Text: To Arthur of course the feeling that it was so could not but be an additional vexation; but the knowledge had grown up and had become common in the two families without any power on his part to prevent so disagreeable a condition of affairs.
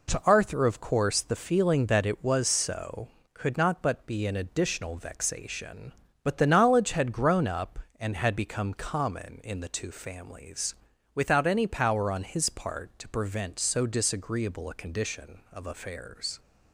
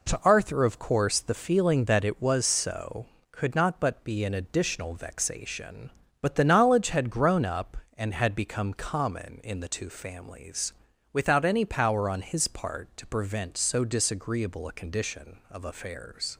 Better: neither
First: pauses between "families" and "without"; at 10.7 s; 0.38 s long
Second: pauses between "families" and "without"; at 10.7 s; 0.38 s long

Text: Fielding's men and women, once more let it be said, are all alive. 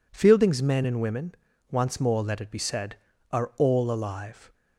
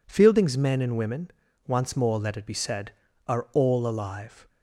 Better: neither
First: none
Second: none

